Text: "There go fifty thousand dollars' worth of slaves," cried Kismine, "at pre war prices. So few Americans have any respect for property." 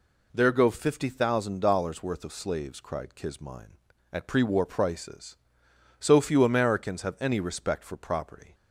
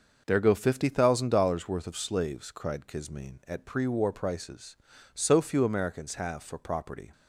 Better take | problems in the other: first | starts louder than the rest; noticeable; until 1.2 s; 6 dB // skips "any respect"; at 6.4 s

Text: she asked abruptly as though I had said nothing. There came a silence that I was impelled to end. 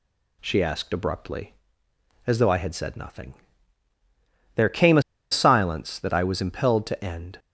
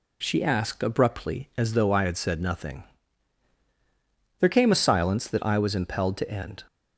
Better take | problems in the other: second | pauses between "a" and "silence"; slight; at 5.0 s; 0.29 s long

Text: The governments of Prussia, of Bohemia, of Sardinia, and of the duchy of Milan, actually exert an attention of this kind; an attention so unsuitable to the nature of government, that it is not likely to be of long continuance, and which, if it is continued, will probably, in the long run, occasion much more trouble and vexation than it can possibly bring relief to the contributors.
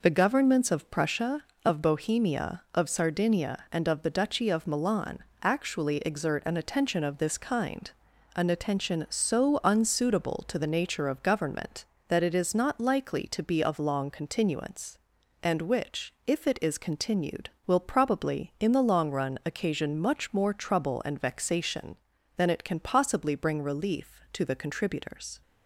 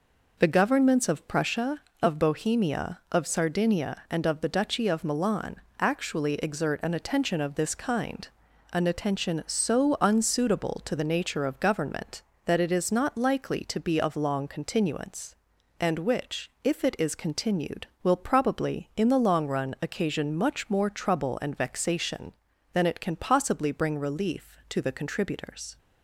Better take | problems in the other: neither | none

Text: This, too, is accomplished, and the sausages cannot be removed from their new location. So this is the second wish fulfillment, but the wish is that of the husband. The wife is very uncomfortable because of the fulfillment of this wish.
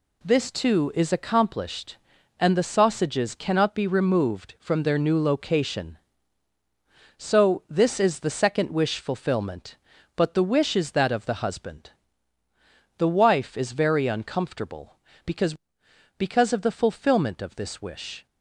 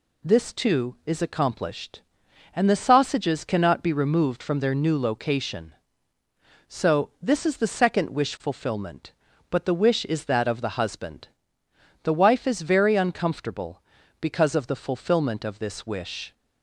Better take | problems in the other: second | says "because" twice; at 16.1 s

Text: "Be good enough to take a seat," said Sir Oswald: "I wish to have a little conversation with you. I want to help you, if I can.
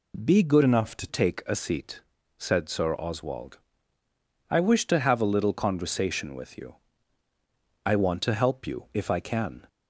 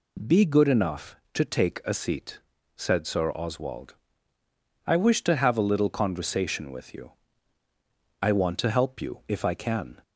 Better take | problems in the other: second | changes voice from "enough" to "to"; from 0.6 to 1.0 s; 0.4 s long

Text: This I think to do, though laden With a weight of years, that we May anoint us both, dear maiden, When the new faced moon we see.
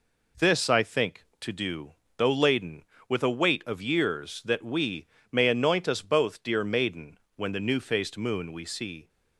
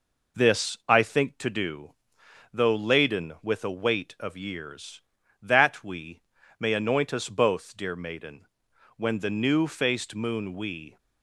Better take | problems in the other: first | pauses between "we" and "May"; at 6.2 s; 0.38 s long; slight in the first // stops before "see"; at 10.9 s

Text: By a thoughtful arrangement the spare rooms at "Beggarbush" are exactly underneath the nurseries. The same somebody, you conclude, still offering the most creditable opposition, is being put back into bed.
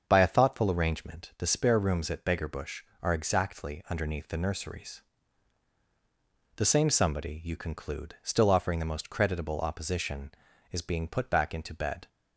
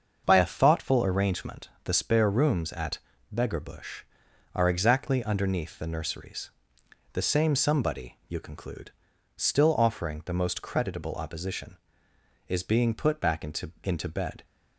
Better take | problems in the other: first | starts louder than the rest; until 1.2 s; 6.5 dB; also in the first // pauses between "at" and "Beggarbush"; slight; at 2.9 s; 0.36 s long // says "into" twice; at 13.8 s

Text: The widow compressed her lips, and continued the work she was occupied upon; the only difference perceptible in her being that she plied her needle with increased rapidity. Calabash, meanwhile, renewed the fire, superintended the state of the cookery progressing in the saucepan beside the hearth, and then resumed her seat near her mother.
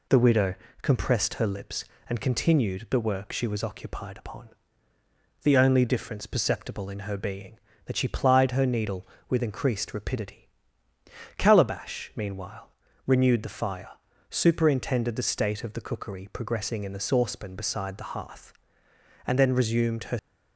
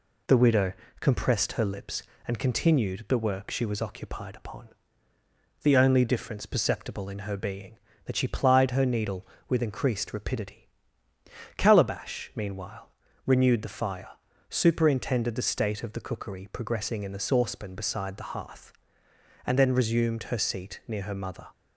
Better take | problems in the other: second | pauses between "widow" and "compressed"; slight; at 0.5 s; 0.30 s long; slight in the second // stops before "seat near her mother"; at 20.1 s

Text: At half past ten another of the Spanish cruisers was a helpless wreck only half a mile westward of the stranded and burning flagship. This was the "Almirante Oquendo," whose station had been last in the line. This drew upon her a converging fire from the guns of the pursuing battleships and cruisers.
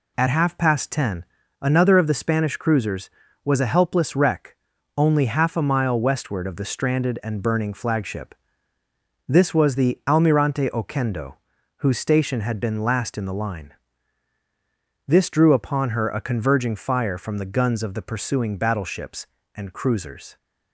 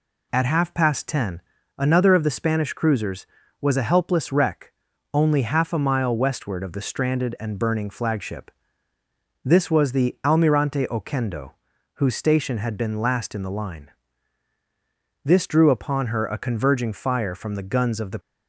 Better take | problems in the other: first | pauses between "ten" and "another"; slight; at 1.4 s; 0.36 s long; slight in the first // pauses between "wreck" and "only"; at 4.7 s; 0.40 s long; also in the first // stops before "pursuing battleships and cruisers"; at 18.1 s

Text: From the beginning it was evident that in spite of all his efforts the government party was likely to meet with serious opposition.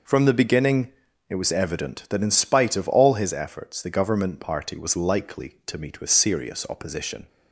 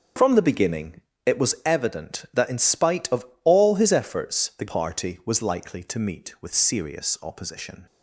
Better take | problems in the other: first | starts louder than the rest; until 1.4 s; 6.5 dB // pauses between "beginning" and "it"; slight; at 1.0 s; 0.26 s long; slight in the first // pauses between "of" and "all"; slight; at 3.2 s; 0.20 s long // skips "government"; at 4.6 s

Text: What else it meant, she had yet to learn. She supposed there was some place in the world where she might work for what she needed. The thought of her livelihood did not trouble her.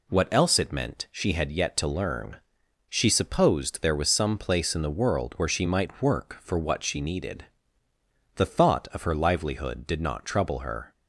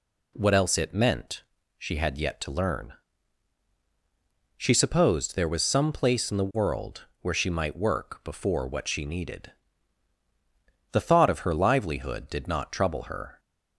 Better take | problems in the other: first | pauses between "world" and "where"; slight; at 7.0 s; 0.16 s long // says "before" for "for"; at 8.2 s

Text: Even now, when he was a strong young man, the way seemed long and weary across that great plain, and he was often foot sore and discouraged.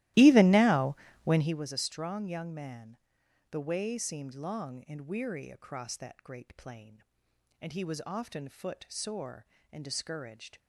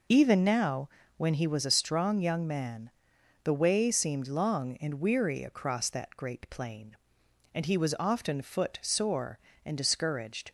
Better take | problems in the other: second | starts louder than the rest; strong; until 1.6 s; 16.5 dB

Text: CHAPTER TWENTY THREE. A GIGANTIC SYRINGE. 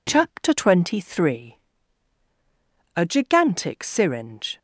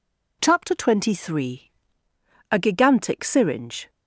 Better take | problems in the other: neither | none

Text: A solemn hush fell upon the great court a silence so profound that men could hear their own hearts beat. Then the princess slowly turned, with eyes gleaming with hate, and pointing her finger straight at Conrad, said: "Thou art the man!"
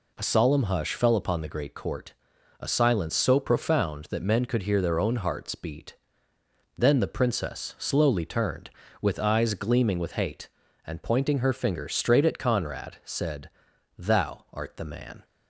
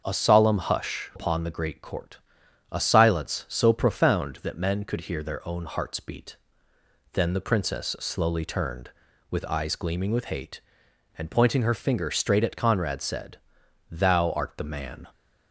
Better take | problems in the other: first | starts louder than the rest; until 1.0 s; 6.5 dB // skips "fell"; at 1.1 s // pauses between "court" and "a"; noticeable; at 2.1 s; 0.56 s long; noticeable in the first

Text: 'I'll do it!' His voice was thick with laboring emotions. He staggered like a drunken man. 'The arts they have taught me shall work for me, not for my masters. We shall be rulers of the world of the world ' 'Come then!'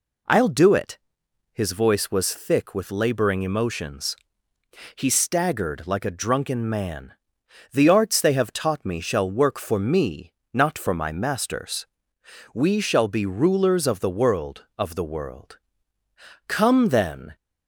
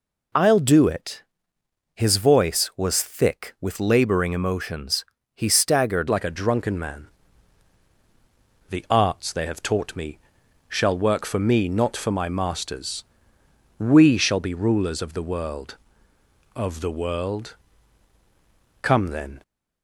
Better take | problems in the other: first | changes voice at "like"; from 6.0 s on; 13.4 s long // pauses between "me" and "shall"; noticeable; at 10.1 s; 0.50 s long

